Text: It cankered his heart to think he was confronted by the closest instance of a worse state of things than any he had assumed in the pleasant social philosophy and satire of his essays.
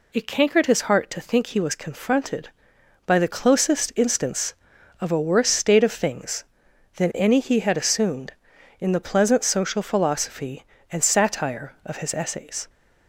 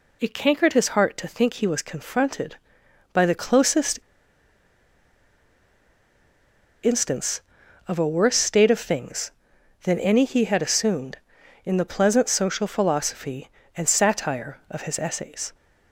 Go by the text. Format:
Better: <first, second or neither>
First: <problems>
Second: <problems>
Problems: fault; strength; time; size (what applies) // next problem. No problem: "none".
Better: first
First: none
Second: pauses between "closest" and "instance"; strong; at 3.9 s; 2.8 s long